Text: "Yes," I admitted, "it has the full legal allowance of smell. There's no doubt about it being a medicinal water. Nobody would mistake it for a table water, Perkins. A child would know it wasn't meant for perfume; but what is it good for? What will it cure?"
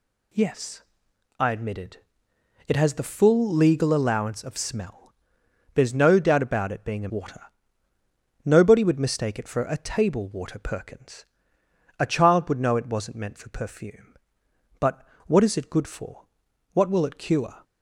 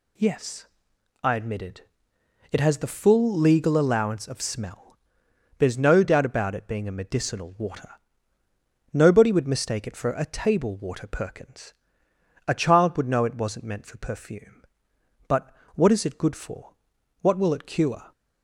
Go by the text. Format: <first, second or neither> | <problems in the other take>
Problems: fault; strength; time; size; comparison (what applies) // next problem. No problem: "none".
second | skips "medicinal"; at 7.0 s // pauses between "but" and "what"; slight; at 15.0 s; 0.22 s long; slight in the second